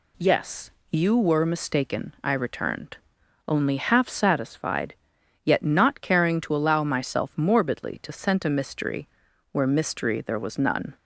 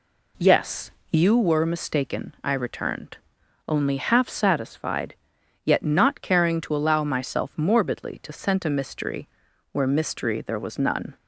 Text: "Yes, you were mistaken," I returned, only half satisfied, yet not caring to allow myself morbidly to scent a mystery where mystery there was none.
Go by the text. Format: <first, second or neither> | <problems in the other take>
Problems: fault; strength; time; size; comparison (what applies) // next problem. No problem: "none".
first | starts louder than the rest; slight; until 1.4 s; 3 dB // pauses between "mystery" and "where"; at 9.2 s; 0.42 s long; also in the first